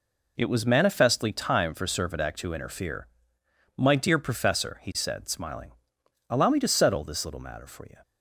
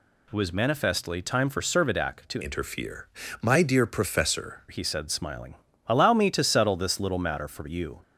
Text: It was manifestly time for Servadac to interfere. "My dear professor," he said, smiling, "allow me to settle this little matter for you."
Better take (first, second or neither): first